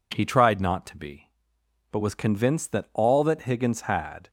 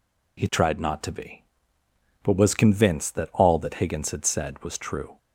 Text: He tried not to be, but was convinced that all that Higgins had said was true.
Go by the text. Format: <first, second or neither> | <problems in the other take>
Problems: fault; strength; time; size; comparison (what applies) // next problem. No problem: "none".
second | stops before "said was true"; at 4.2 s